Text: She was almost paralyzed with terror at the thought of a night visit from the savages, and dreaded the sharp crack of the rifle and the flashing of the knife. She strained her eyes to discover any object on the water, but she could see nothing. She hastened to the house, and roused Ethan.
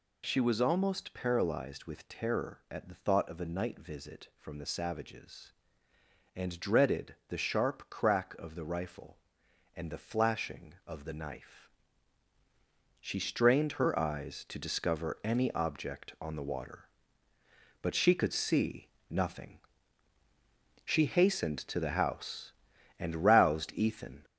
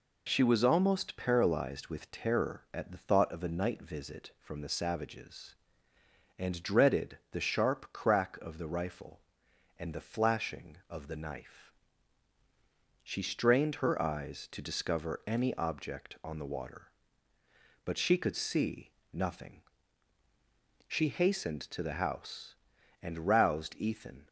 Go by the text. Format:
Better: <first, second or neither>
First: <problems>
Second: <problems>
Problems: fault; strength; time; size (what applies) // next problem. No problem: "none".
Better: second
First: gets louder; noticeable; throughout; 4.5 dB // pauses between "see" and "nothing"; slight; at 18.8 s; 0.22 s long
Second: pauses between "see" and "nothing"; slight; at 18.9 s; 0.22 s long